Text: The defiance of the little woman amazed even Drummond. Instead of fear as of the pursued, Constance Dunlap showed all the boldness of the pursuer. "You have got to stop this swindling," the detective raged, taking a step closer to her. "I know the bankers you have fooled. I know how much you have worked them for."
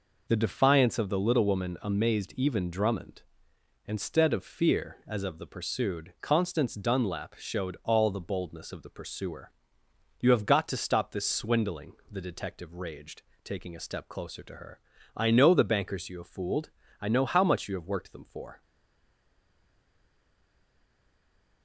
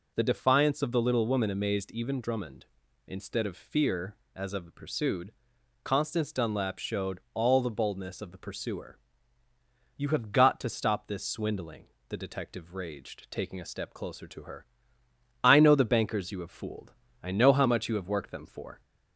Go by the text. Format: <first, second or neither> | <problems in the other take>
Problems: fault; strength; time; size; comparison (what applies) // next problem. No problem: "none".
second | stays silent after the last word; strong; from 18.6 s on; 3.0 s long